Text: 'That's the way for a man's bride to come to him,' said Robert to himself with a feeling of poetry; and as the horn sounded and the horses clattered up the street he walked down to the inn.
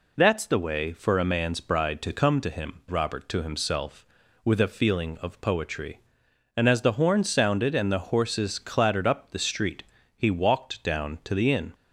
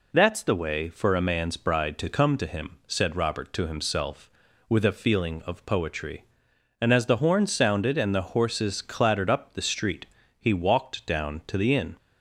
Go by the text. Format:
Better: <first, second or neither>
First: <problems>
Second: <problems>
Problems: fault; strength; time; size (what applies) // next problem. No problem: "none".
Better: second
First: skips "said"; at 2.8 s // pauses between "street" and "he"; slight; at 9.8 s; 0.34 s long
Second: pauses between "street" and "he"; slight; at 10.0 s; 0.34 s long